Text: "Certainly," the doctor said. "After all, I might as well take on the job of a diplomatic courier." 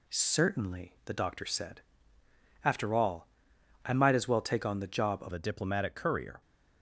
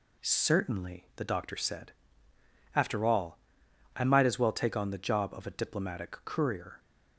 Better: second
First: changes voice at "a"; from 5.3 s on; 1.1 s long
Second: none

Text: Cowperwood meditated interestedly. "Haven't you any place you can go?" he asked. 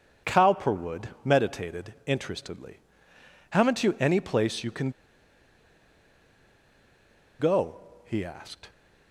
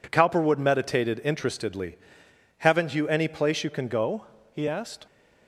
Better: second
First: pauses between "Cowperwood" and "meditated"; slight; at 1.0 s; 0.16 s long // pauses between "can" and "go"; strong; at 4.8 s; 2.4 s long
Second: none

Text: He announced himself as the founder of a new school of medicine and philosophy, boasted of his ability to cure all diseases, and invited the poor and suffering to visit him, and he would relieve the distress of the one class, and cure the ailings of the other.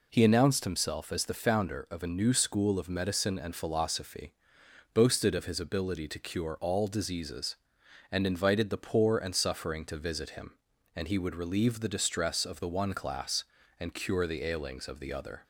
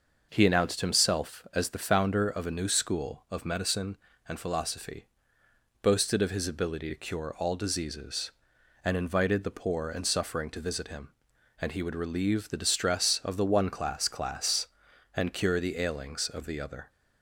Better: first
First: none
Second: starts louder than the rest; noticeable; until 1.3 s; 6 dB // says "class" twice; at 14.0 s

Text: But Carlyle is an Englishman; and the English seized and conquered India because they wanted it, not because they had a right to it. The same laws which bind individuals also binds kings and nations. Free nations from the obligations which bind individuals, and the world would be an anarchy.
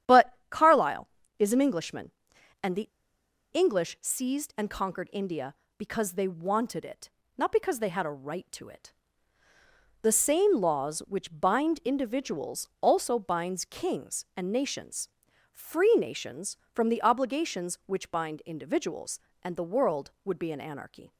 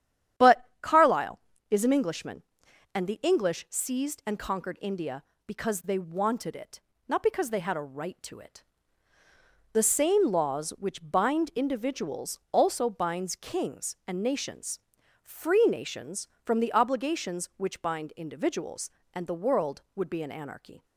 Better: second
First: starts louder than the rest; strong; until 1.5 s; 9.5 dB // pauses between "the" and "English"; noticeable; at 2.8 s; 0.66 s long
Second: starts louder than the rest; strong; until 1.8 s; 9.5 dB

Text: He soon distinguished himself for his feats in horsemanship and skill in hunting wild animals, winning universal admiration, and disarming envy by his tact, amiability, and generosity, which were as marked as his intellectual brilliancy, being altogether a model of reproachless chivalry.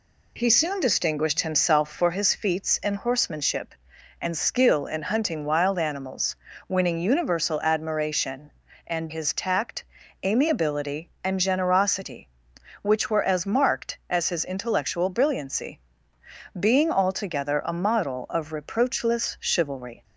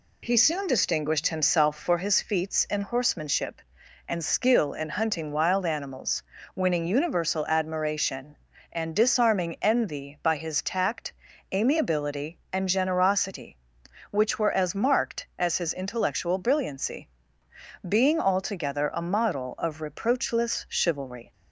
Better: second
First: skips "disarming envy by"; at 9.0 s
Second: none

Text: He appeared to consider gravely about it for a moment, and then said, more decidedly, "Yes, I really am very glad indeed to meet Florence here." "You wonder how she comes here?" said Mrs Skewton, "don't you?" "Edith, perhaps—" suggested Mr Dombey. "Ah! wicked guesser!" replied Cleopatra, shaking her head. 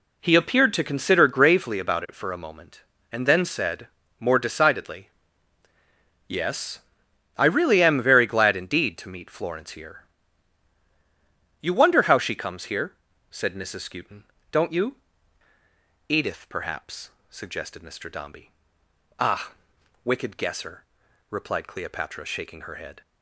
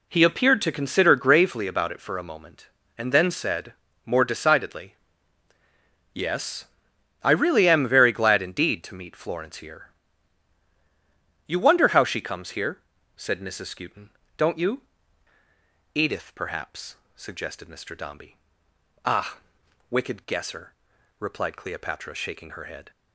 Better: neither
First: none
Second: none

